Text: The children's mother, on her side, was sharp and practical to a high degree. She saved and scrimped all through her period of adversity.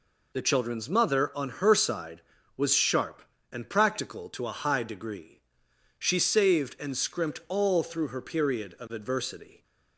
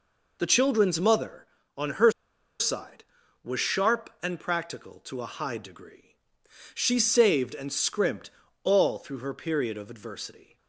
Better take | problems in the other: first | pauses between "her" and "side"; noticeable; at 2.0 s; 0.50 s long // pauses between "scrimped" and "all"; slight; at 8.3 s; 0.32 s long

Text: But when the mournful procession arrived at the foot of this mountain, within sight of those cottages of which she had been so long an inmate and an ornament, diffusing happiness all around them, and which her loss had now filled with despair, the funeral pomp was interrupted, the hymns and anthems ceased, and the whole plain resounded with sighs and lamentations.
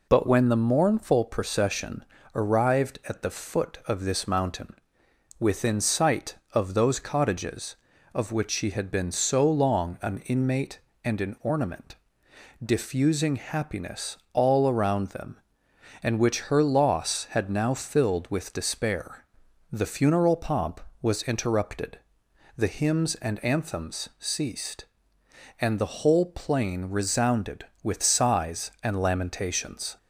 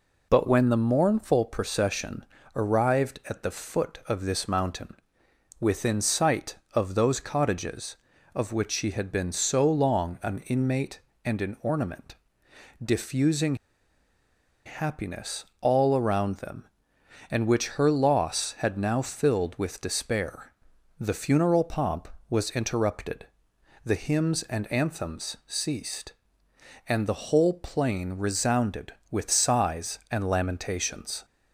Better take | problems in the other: first | pauses between "procession" and "arrived"; slight; at 2.2 s; 0.30 s long; slight in the first // pauses between "diffusing" and "happiness"; at 13.5 s; 1.1 s long // pauses between "happiness" and "all"; slight; at 15.4 s; 0.16 s long; slight in the first

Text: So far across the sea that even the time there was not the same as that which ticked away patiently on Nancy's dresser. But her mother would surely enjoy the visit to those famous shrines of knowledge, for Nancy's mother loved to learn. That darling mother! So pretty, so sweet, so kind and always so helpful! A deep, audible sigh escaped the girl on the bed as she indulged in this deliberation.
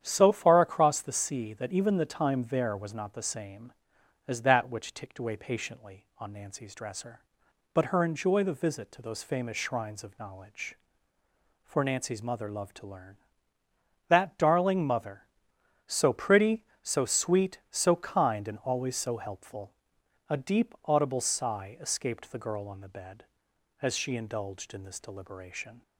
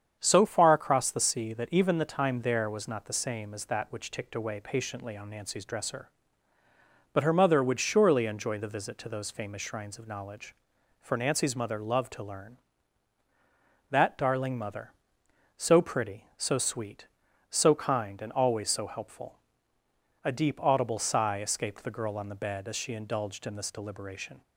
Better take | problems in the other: second | starts louder than the rest; strong; until 1.0 s; 9.5 dB; strong in the second // skips "mother would surely"; at 8.0 s

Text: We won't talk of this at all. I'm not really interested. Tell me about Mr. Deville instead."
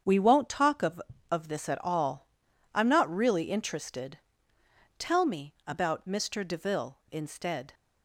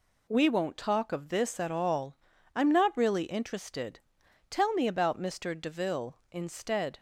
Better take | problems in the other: second | starts louder than the rest; strong; until 1.3 s; 7.5 dB // says "of" twice; at 1.2 s

